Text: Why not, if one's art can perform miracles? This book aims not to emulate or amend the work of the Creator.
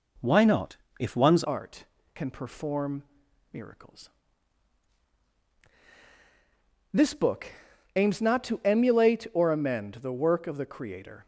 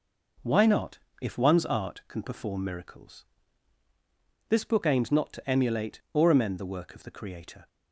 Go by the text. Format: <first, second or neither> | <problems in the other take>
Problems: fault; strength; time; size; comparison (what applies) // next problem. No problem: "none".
second | changes voice at "art"; from 1.4 s on; 9.8 s long // pauses between "perform" and "miracles"; noticeable; at 3.0 s; 0.48 s long // pauses between "book" and "aims"; noticeable; at 7.4 s; 0.48 s long